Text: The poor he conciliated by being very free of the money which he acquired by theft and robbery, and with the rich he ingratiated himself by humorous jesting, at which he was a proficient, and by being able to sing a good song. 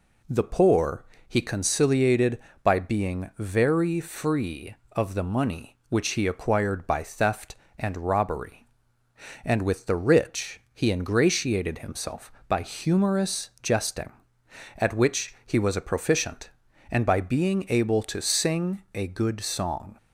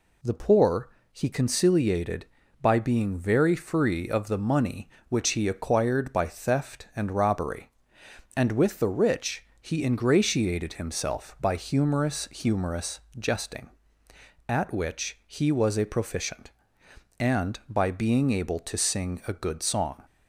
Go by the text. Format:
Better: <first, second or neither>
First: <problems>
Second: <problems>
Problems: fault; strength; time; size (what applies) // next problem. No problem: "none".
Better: first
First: pauses between "poor" and "he"; slight; at 1.0 s; 0.24 s long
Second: pauses between "poor" and "he"; slight; at 0.8 s; 0.22 s long // pauses between "rich" and "he"; slight; at 9.4 s; 0.18 s long // says "humorous" twice; at 12.3 s